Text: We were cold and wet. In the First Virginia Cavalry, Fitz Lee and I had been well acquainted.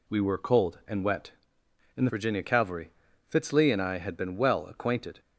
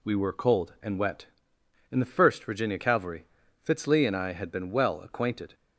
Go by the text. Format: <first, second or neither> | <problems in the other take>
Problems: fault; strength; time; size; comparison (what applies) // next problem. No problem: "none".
second | skips "First"; at 2.1 s